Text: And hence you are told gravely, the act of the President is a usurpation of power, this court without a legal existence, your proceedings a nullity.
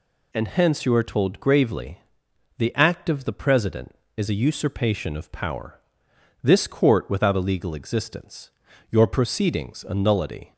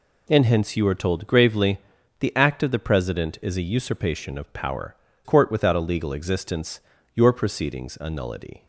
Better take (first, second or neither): first